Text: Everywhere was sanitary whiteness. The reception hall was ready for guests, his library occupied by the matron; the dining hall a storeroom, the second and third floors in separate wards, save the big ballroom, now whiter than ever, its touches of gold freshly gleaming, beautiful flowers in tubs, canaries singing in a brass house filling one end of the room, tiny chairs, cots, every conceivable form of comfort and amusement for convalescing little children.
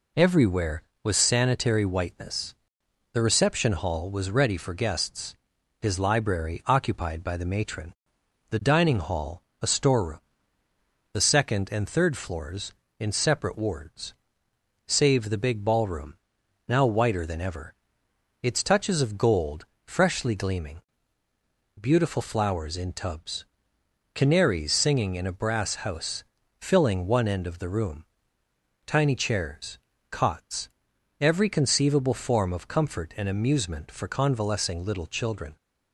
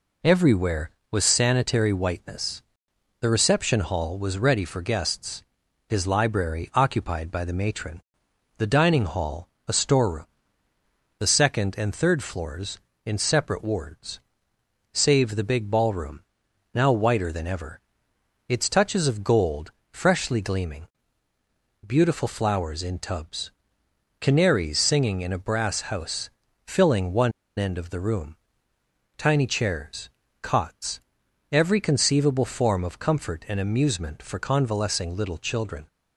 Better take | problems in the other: first | pauses between "hall" and "a"; slight; at 9.4 s; 0.18 s long; slight in the first // pauses between "gold" and "freshly"; slight; at 19.7 s; 0.18 s long; slight in the first // pauses between "house" and "filling"; at 26.2 s; 0.38 s long; also in the first // pauses between "one" and "end"; slight; at 27.3 s; 0.25 s long

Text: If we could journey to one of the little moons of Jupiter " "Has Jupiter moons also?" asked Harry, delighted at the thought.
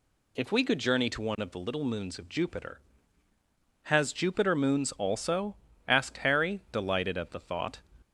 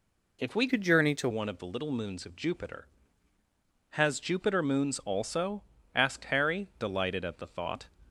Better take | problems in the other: first | changes voice from "could" to "to"; from 0.6 to 1.2 s; 0.6 s long

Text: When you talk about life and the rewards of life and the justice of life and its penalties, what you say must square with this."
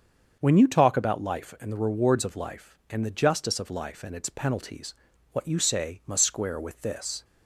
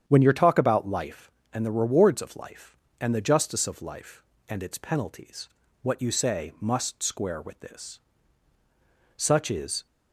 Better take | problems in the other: first | starts louder than the rest; strong; until 1.0 s; 8.5 dB; also in the first // goes on to say "Such is"; noticeable; from 9.1 s on; 0.70 s long

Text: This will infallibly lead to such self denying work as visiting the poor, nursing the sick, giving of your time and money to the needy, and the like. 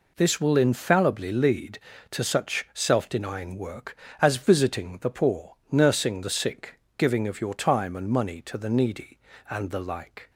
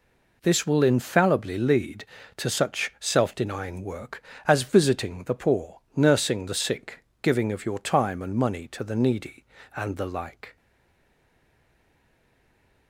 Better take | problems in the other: first | stays silent after the last word; from 10.5 s on; 2.3 s long

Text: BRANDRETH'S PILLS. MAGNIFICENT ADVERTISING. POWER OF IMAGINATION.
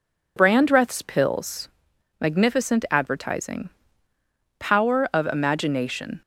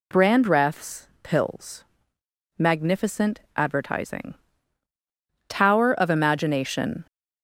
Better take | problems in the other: first | pauses between "MAGNIFICENT" and "ADVERTISING"; slight; at 3.3 s; 0.16 s long // says "Tower" for "POWER"; at 5.4 s

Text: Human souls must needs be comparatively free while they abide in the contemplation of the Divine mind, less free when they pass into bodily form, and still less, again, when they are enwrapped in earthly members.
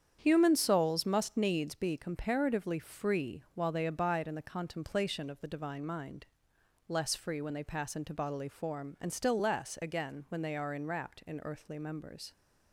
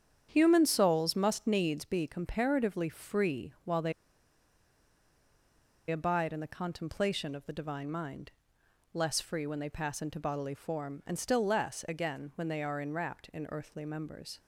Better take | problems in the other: first | starts louder than the rest; strong; until 1.3 s; 8.5 dB; strong in the first // pauses between "they" and "abide"; strong; at 3.9 s; 1.9 s long

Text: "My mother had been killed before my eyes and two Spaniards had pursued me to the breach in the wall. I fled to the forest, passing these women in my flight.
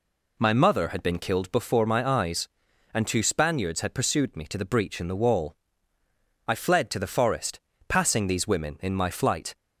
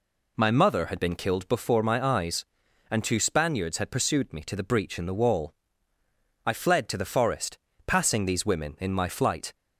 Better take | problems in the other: neither | none

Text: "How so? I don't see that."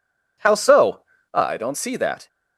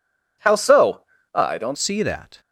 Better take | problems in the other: first | changes voice at "see"; from 1.7 s on; 0.7 s long

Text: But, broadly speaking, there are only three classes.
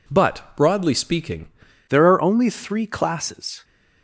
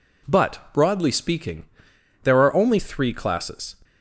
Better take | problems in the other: second | changes voice at "there"; from 1.8 s on; 1.8 s long

